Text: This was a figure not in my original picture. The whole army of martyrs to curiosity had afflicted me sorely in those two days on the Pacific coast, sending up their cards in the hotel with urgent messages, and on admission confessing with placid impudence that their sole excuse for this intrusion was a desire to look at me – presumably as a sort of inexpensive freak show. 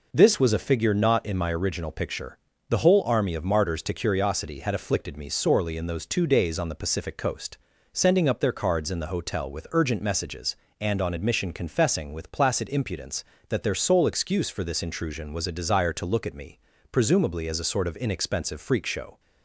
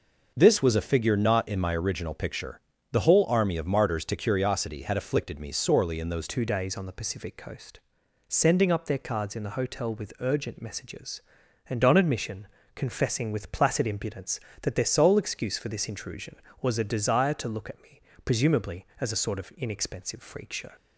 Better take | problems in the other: first | changes voice at "two"; from 6.2 s on; 14.5 s long // pauses between "admission" and "confessing"; slight; at 12.4 s; 0.28 s long

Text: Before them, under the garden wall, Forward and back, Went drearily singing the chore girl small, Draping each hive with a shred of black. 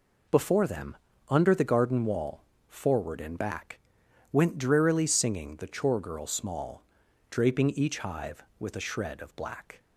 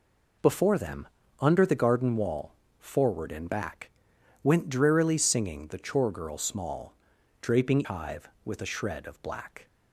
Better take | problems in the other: first | skips "each"; at 7.8 s

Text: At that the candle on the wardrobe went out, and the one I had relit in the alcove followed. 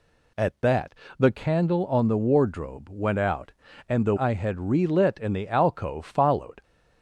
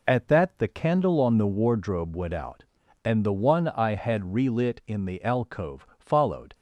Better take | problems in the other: second | pauses between "that" and "the"; slight; at 0.9 s; 0.24 s long // skips "one"; at 4.1 s

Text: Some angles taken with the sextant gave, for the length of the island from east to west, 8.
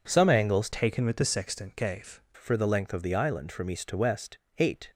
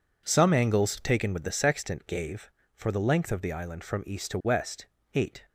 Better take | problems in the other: second | changes voice from "taken" to "gave"; from 0.7 to 2.1 s; 1.4 s long

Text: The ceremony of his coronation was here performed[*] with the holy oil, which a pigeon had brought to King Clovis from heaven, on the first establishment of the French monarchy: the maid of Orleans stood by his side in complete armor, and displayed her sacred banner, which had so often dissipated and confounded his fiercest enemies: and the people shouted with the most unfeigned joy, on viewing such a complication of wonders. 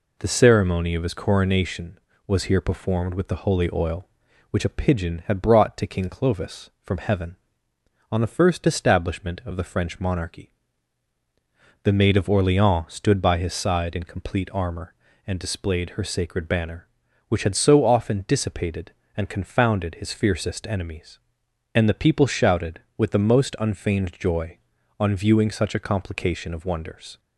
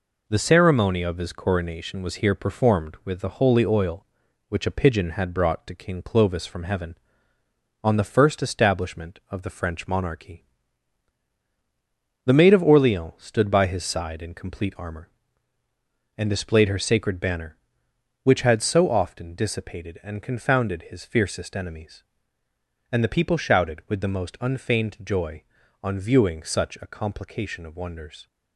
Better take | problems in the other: neither | none

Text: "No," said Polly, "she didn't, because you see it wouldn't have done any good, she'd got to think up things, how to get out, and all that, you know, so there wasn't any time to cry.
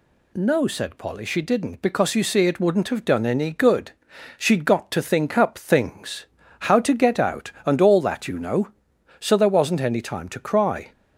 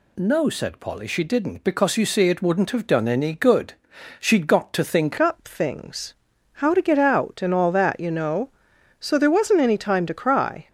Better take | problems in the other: first | changes voice at "up"; from 5.1 s on; 5.5 s long

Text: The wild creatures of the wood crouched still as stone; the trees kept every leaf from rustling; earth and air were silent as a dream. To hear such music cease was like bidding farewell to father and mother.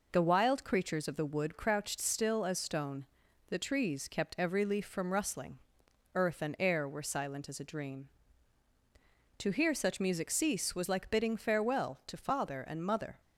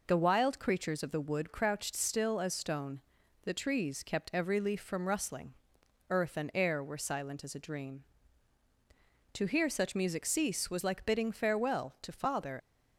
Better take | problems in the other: first | stops before "and mother"; at 12.5 s

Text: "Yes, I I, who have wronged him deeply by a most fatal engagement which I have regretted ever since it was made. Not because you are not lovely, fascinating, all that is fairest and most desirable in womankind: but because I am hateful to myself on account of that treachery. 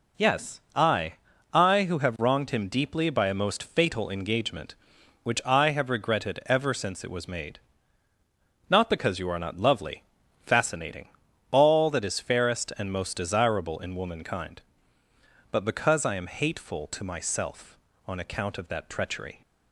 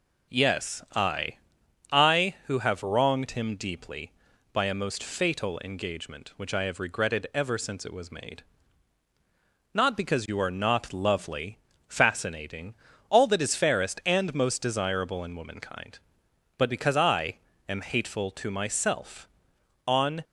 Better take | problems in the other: first | pauses between "I" and "I"; noticeable; at 1.3 s; 0.52 s long; also in the first // pauses between "I" and "am"; slight; at 17.3 s; 0.30 s long // stops before "account of that treachery"; at 20.2 s

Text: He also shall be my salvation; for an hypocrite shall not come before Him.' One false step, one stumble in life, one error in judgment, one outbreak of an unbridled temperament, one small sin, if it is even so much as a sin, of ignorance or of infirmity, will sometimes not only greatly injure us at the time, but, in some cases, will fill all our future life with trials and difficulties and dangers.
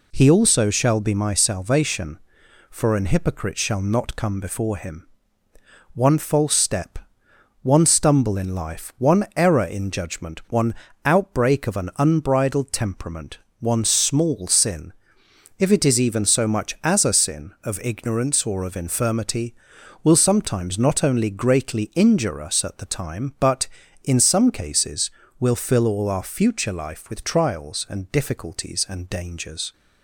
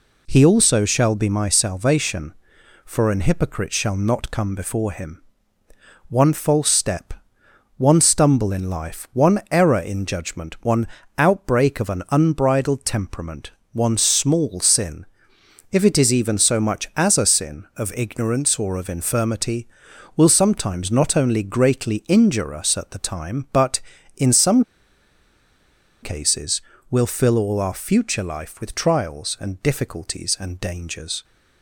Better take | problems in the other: first | pauses between "one" and "outbreak"; slight; at 10.8 s; 0.30 s long; slight in the first // pauses between "some" and "cases"; strong; at 24.6 s; 1.3 s long

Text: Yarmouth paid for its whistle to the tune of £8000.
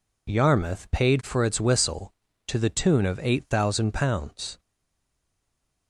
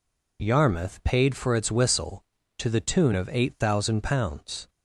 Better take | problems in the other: second | stays silent after the last word; noticeable; from 4.5 s on; 1.3 s long

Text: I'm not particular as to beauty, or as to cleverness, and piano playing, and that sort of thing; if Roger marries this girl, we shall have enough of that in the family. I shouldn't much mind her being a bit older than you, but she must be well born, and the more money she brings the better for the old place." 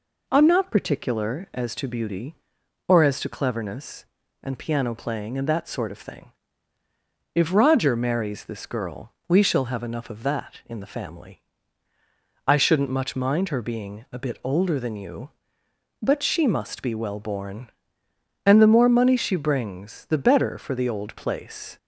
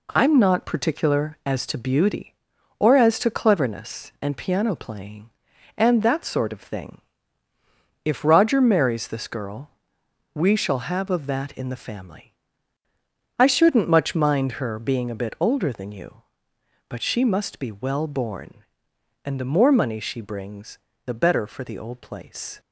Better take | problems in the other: first | skips "enough"; at 11.1 s // pauses between "brings" and "the"; slight; at 20.7 s; 0.26 s long

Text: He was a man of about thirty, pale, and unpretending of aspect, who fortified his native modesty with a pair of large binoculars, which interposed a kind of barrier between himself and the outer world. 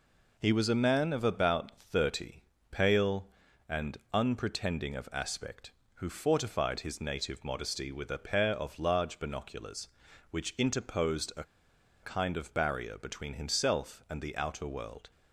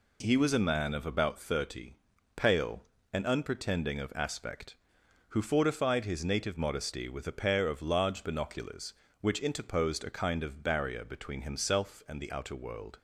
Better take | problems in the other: second | pauses between "and" and "unpretending"; slight; at 3.9 s; 0.16 s long // pauses between "a" and "kind"; noticeable; at 11.4 s; 0.59 s long

